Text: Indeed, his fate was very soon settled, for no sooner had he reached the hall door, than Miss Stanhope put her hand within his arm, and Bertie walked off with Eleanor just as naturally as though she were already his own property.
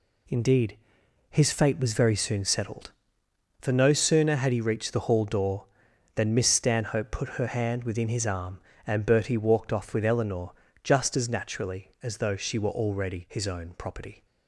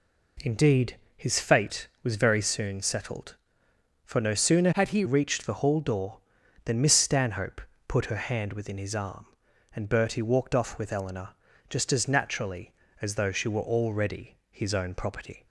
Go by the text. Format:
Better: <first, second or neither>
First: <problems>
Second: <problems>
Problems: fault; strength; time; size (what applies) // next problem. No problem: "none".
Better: first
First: pauses between "Eleanor" and "just"; slight; at 10.5 s; 0.30 s long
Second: changes voice from "had" to "he"; from 4.7 to 5.0 s; 0.3 s long // pauses between "Stanhope" and "put"; slight; at 7.6 s; 0.28 s long // pauses between "Eleanor" and "just"; at 11.3 s; 0.38 s long // pauses between "already" and "his"; slight; at 14.3 s; 0.16 s long